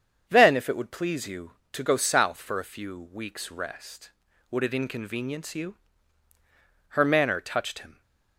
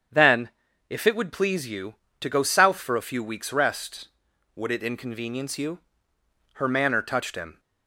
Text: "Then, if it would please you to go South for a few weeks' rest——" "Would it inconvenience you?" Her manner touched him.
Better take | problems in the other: neither | starts louder than the rest; strong; the same in both

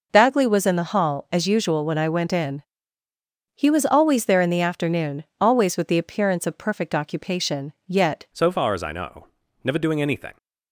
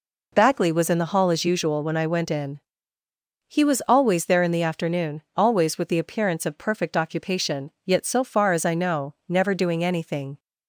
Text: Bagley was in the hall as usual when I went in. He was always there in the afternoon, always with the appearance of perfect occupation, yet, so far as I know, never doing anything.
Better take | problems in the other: second | changes voice at "so"; from 8.3 s on; 2.0 s long

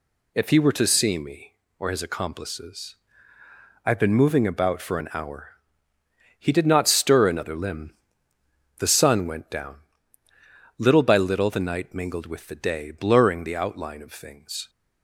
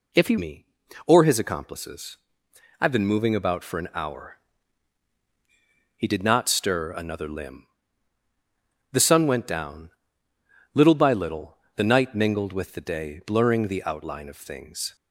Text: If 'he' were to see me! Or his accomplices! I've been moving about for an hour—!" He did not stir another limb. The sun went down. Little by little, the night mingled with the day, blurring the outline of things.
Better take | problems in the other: first | skips "were to see"; at 0.3 s

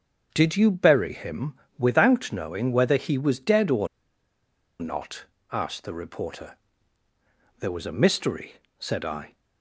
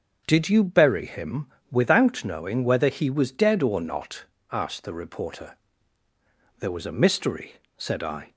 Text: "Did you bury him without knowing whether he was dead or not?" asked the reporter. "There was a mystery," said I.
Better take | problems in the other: second | starts louder than the rest; until 1.3 s; 6.5 dB; also in the second // pauses between "him" and "without"; slight; at 1.5 s; 0.22 s long; slight in the second // pauses between "or" and "not"; noticeable; at 3.8 s; 0.93 s long

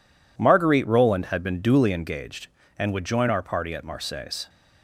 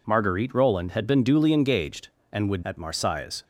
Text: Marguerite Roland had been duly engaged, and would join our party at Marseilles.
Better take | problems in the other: first | skips "join our party"; at 2.6 s

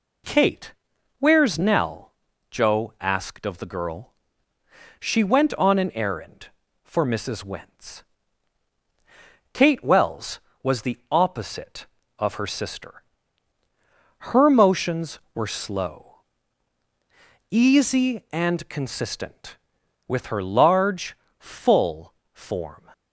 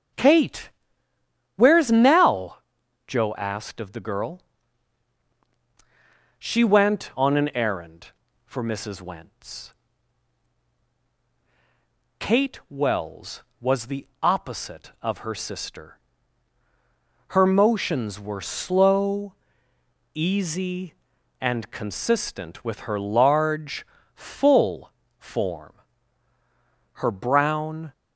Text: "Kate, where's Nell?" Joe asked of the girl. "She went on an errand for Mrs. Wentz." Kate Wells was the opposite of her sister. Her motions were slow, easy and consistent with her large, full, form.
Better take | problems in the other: first | goes on to say "Her brown"; noticeable; from 26.9 s on; 0.98 s long

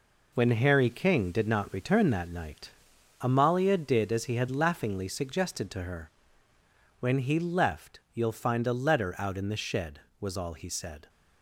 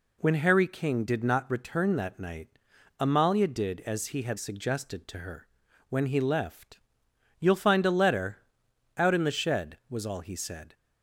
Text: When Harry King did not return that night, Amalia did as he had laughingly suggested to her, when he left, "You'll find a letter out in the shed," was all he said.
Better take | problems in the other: first | skips "laughingly"; at 4.3 s // pauses between "letter" and "out"; noticeable; at 8.3 s; 0.60 s long

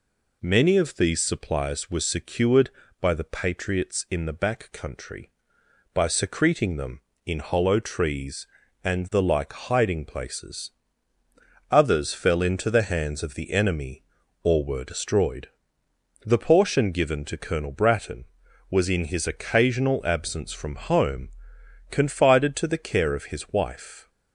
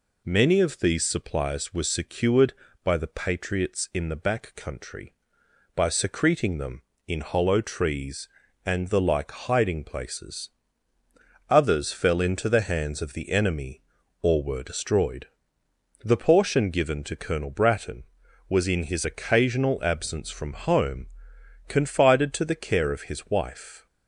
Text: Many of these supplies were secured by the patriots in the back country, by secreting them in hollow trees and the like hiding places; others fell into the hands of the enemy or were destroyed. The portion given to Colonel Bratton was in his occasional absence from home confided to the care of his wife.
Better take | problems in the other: neither | pauses between "home" and "confided"; noticeable; the same in both

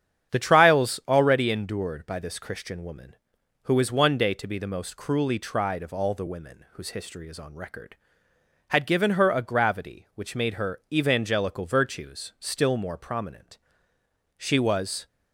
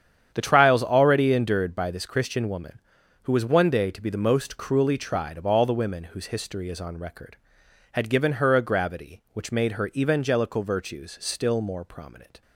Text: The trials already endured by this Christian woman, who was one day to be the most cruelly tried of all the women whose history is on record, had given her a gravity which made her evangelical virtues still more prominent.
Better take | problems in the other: second | starts louder than the rest; strong; until 1.3 s; 9 dB; strong in the second // goes on to say "She was"; noticeable; from 14.3 s on; 0.70 s long

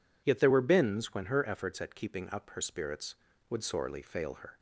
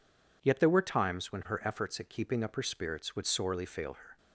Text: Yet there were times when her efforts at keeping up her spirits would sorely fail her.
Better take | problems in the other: second | says "bins" for "times"; at 0.6 s

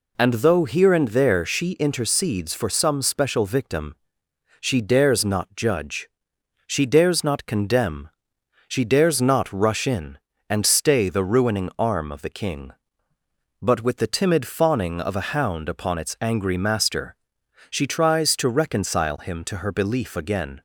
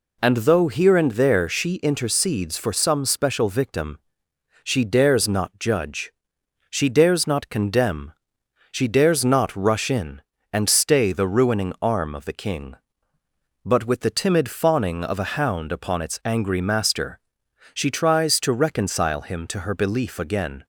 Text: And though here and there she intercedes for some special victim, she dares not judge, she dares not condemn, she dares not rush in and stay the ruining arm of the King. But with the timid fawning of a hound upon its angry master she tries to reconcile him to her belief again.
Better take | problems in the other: neither | pauses between "master" and "she"; noticeable; the same in both

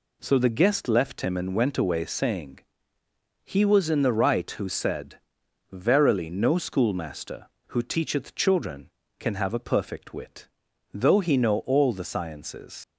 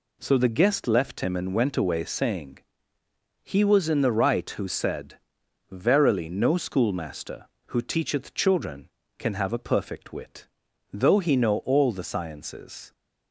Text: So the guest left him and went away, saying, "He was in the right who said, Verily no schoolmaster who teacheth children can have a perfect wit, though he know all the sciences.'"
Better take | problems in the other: second | leaves "sciences" unfinished; at 12.8 s; 90 ms

